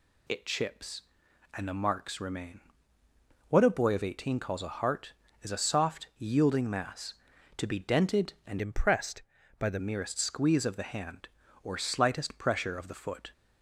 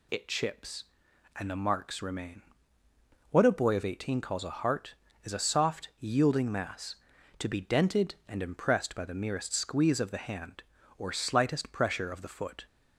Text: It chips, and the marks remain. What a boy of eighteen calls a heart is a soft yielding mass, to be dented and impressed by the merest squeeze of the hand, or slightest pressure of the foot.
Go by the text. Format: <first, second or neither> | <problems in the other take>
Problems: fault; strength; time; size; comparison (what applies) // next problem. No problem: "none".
second | changes voice from "impressed" to "the"; from 8.6 to 9.7 s; 1.1 s long